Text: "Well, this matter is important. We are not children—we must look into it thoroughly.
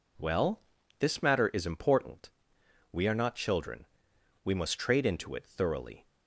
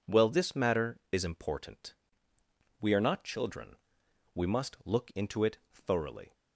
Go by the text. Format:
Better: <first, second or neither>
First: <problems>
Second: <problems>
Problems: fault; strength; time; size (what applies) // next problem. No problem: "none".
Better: second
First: says "trade" for "look"; at 4.7 s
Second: none